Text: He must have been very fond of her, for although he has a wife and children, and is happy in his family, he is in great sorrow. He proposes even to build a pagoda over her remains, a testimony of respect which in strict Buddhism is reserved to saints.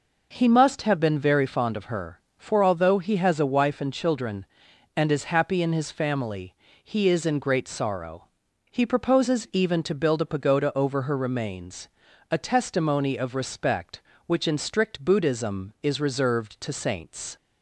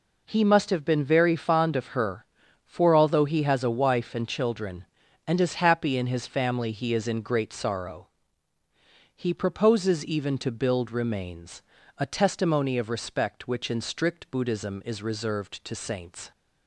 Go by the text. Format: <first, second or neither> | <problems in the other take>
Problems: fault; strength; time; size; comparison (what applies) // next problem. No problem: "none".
first | skips "a pagoda over her"; at 10.9 s